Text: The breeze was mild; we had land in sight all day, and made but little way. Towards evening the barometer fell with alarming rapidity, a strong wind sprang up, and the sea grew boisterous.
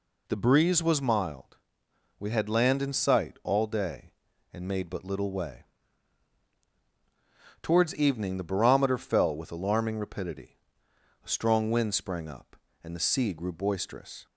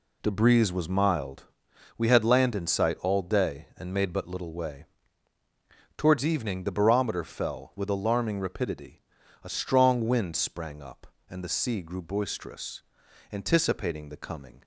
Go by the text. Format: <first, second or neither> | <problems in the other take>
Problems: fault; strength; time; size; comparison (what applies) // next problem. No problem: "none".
first | goes on to say "Anticipating the coming"; noticeable; from 13.3 s on; 1.3 s long